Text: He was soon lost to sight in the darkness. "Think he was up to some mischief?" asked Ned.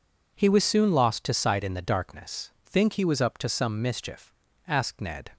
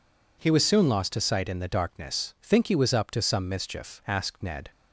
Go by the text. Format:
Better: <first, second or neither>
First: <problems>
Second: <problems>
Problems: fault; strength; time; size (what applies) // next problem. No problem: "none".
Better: neither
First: none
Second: none